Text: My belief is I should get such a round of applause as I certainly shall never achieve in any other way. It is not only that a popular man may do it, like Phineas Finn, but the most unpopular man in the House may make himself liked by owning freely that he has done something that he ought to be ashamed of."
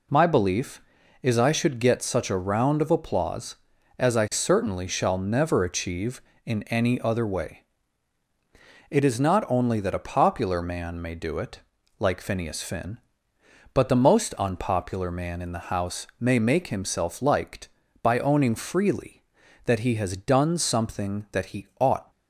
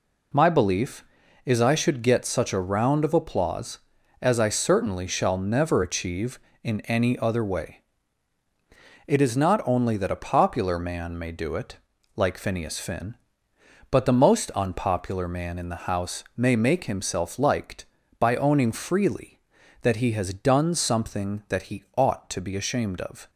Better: second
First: stops before "to be ashamed of"; at 22.1 s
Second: none

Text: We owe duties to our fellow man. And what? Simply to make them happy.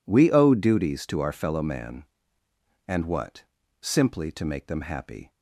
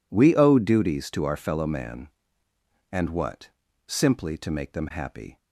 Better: neither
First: none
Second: none

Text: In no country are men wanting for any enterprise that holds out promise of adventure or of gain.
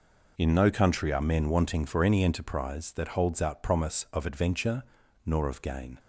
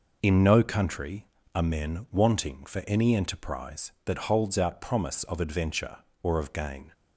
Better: second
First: says "nor" for "or"; at 5.2 s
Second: none

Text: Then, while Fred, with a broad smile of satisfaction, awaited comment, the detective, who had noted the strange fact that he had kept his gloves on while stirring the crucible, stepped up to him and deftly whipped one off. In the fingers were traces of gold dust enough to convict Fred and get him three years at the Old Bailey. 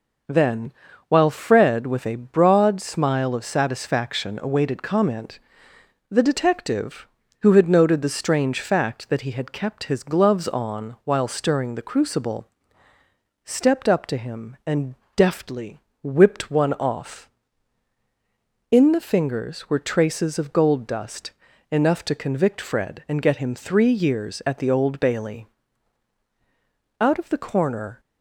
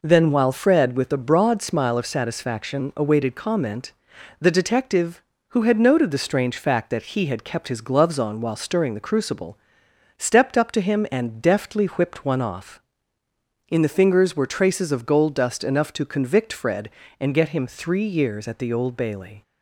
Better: second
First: pauses between "and" and "deftly"; slight; at 14.9 s; 0.22 s long // pauses between "deftly" and "whipped"; slight; at 15.7 s; 0.22 s long // pauses between "dust" and "enough"; at 21.3 s; 0.38 s long // goes on to say "Out of the corner"; noticeable; from 26.9 s on; 1.0 s long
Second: none

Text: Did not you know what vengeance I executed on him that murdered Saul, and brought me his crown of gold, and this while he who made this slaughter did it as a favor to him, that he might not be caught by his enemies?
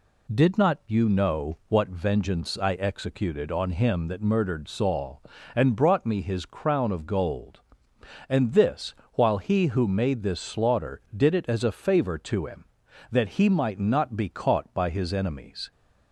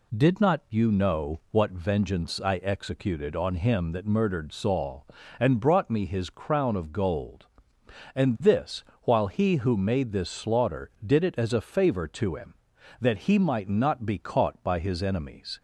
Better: neither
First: pauses between "this" and "while"; slight; at 8.9 s; 0.20 s long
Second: pauses between "this" and "while"; slight; at 8.8 s; 0.20 s long

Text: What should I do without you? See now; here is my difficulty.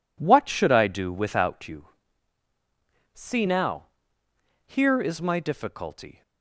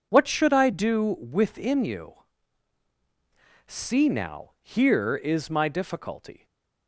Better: first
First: none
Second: says "within" for "without"; at 1.1 s // stays silent after the last word; slight; from 6.3 s on; 0.5 s long

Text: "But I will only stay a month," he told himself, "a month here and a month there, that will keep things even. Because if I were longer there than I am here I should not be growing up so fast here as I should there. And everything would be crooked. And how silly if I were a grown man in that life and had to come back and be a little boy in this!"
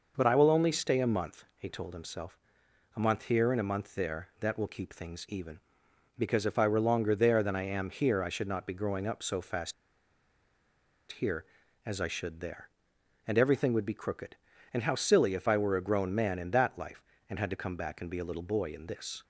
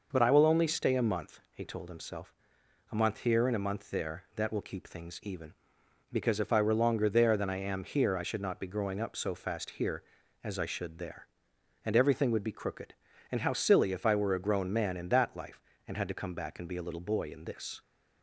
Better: second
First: pauses between "fast" and "here"; strong; at 9.7 s; 1.3 s long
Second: none

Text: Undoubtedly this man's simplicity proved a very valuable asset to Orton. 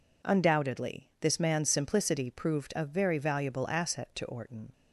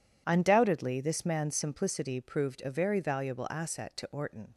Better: neither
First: none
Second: none

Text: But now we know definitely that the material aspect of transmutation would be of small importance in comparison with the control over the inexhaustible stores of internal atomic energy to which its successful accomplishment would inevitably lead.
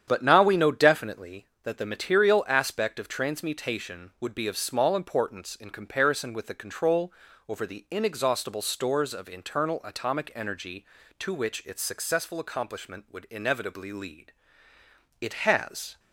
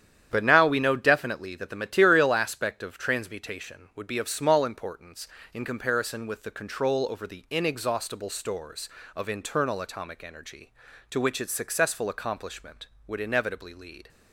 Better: second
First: starts louder than the rest; strong; until 1.0 s; 9 dB // pauses between "control" and "over"; slight; at 7.1 s; 0.34 s long // goes on to say "It has"; noticeable; from 15.2 s on; 0.78 s long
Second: starts louder than the rest; strong; until 1.3 s; 10 dB

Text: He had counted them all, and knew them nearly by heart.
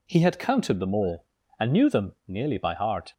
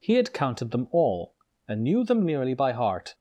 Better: neither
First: none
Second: none

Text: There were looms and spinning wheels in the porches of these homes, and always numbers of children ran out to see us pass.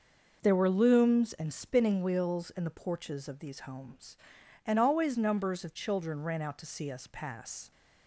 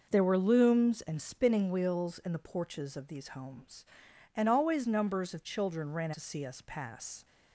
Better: first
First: none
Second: skips "out"; at 6.1 s

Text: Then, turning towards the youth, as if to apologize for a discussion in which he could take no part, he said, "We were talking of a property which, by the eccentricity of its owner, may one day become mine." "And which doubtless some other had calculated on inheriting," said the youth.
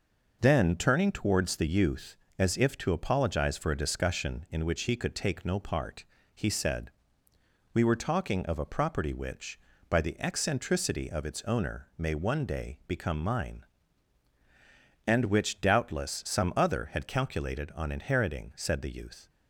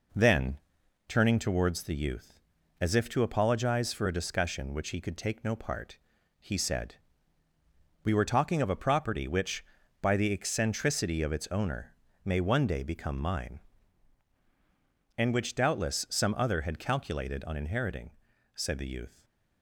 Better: first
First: none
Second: skips "in"; at 4.7 s // stays silent after the last word; slight; from 19.0 s on; 0.6 s long

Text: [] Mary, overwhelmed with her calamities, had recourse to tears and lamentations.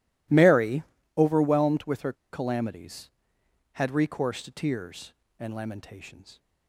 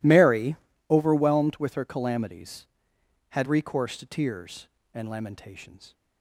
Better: second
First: pauses between "her" and "calamities"; slight; at 2.1 s; 0.18 s long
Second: none

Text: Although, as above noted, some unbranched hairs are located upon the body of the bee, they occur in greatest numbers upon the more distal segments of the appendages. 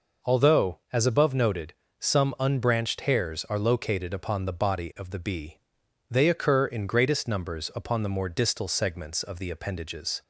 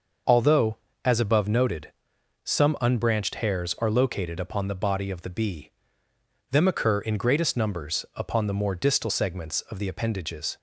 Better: first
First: none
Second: starts louder than the rest; noticeable; until 1.5 s; 6 dB // says "them" for "they"; at 6.5 s

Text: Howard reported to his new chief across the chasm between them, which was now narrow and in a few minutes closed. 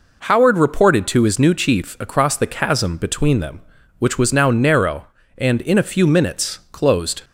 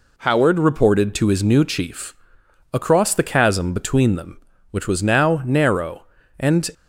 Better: first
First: none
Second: pauses between "chief" and "across"; noticeable; at 2.1 s; 0.58 s long // stops before "in a few minutes closed"; at 6.7 s

